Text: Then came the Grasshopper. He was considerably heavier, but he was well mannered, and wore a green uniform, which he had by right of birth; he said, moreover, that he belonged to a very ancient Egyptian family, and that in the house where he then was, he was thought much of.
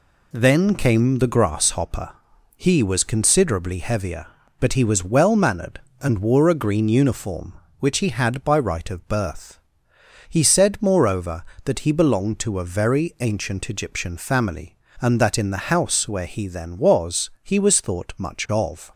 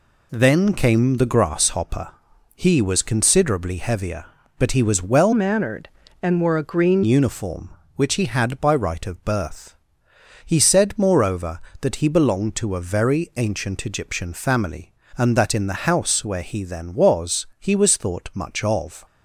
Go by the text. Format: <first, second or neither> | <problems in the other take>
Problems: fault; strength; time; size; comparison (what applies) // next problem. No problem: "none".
first | changes voice from "mannered" to "green"; from 5.3 to 7.0 s; 1.7 s long